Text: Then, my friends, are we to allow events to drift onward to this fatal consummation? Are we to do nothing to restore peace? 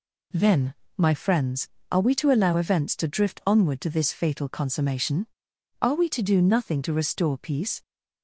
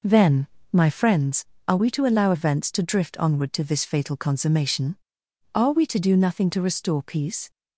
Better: first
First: none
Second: starts louder than the rest; noticeable; until 1.1 s; 5 dB

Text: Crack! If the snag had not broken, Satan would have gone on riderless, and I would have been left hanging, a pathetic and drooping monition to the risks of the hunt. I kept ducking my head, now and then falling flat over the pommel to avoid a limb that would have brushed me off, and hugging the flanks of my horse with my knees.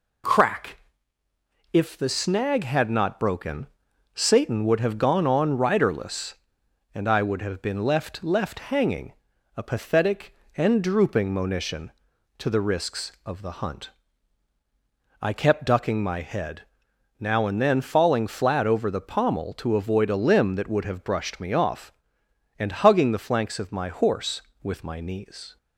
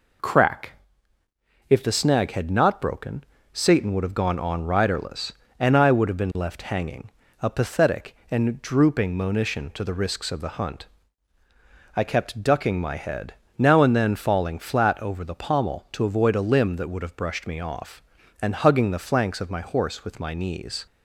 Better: second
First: says "left" twice; at 8.2 s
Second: none

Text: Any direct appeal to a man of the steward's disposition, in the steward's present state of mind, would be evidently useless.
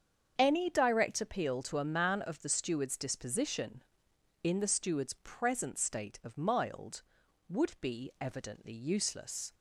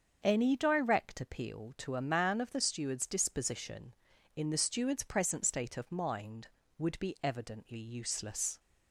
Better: second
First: starts louder than the rest; strong; until 1.3 s; 7.5 dB // says "mild" for "mind"; at 6.3 s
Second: starts louder than the rest; until 1.2 s; 7 dB

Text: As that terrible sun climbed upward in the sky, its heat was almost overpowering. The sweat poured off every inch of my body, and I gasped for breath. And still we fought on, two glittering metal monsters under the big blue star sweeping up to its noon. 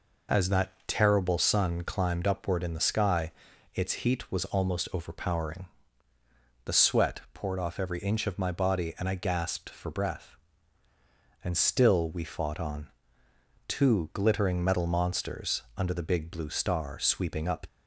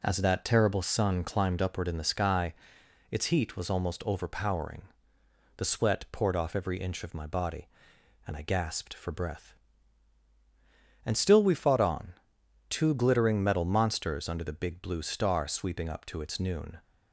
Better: second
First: stops before "to its noon"; at 17.6 s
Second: none

